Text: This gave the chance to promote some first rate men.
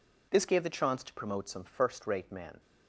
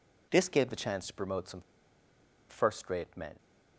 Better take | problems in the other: first | pauses between "some" and "first"; noticeable; at 1.6 s; 0.88 s long

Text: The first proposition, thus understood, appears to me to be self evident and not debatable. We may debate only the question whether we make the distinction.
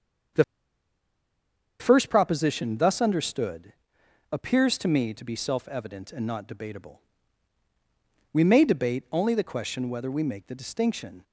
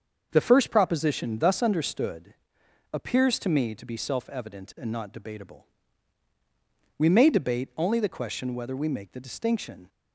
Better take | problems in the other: second | starts louder than the rest; until 2.7 s; 7 dB; also in the second // pauses between "The" and "first"; strong; at 0.4 s; 1.3 s long

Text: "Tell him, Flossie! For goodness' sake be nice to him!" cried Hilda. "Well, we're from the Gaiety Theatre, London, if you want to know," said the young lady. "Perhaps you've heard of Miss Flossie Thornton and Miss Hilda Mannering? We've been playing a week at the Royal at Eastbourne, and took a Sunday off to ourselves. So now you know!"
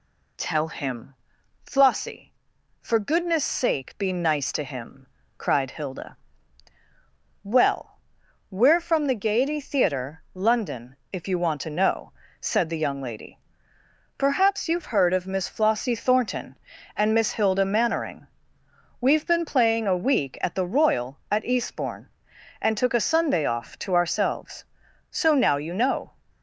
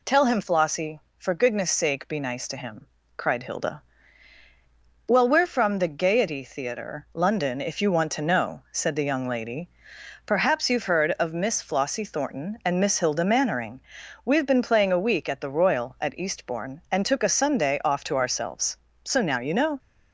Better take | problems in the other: neither | none

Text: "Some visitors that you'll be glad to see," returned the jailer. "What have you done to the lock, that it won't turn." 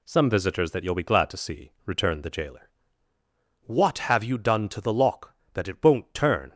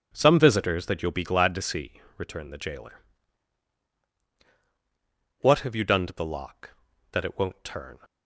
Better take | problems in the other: neither | none

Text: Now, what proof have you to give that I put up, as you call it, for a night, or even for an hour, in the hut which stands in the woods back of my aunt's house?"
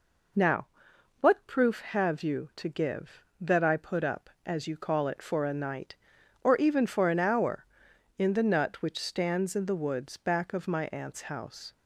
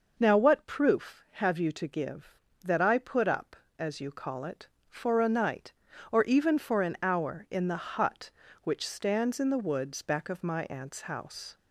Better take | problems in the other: second | says "nut" for "hut"; at 8.4 s

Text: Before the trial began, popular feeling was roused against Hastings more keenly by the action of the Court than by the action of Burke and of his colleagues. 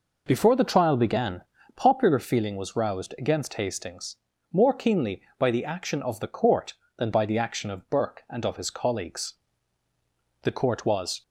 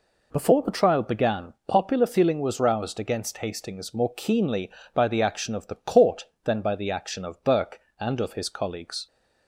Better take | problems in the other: second | pauses between "Hastings" and "more"; slight; at 4.1 s; 0.34 s long // goes on to say "The Court was"; noticeable; from 10.4 s on; 0.80 s long

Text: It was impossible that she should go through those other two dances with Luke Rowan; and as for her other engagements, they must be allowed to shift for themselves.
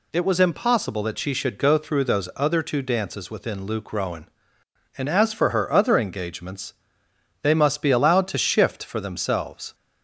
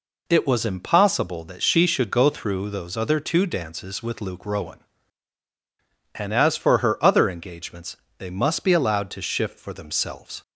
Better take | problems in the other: second | says "within" for "with"; at 3.3 s

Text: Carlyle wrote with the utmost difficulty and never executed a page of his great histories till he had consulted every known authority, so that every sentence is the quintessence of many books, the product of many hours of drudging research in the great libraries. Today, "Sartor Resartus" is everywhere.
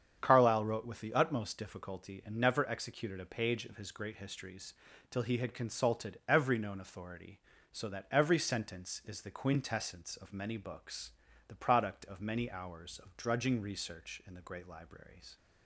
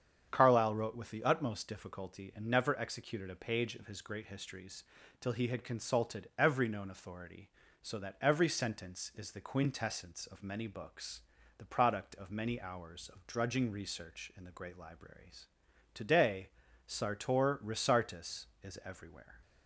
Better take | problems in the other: second | starts louder than the rest; strong; until 1.2 s; 8 dB; strong in the second // pauses between "histories" and "till"; slight; at 4.7 s; 0.36 s long; slight in the second // stops before "Today Sartor Resartus is everywhere"; at 15.3 s

